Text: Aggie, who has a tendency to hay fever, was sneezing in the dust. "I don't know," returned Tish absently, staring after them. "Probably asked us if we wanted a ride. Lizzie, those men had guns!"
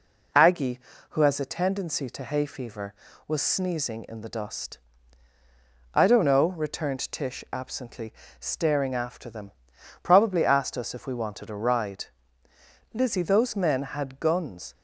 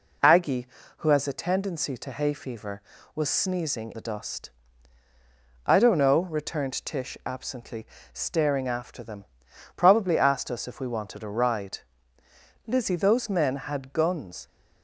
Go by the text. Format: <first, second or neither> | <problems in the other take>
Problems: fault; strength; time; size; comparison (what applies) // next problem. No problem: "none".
first | skips "in"; at 3.9 s